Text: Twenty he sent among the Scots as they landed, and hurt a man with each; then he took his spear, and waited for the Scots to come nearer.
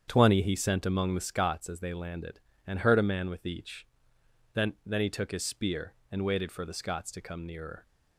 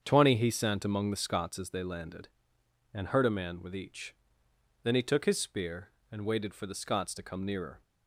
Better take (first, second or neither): second